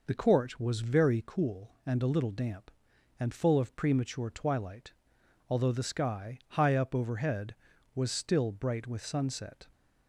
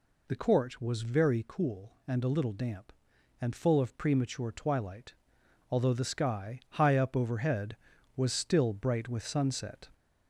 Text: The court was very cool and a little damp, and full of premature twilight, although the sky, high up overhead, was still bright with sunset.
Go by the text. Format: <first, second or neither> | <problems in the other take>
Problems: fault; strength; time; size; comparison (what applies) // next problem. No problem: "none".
first | gets louder; slight; throughout; 2 dB